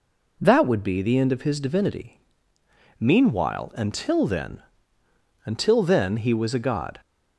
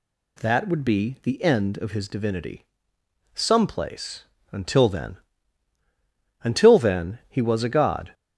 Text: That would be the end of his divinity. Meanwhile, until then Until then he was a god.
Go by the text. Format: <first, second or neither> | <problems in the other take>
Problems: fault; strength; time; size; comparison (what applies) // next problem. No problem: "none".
first | says "Someplace" for "Meanwhile"; at 3.3 s // pauses between "then" and "Until"; strong; at 5.1 s; 1.2 s long; noticeable in the first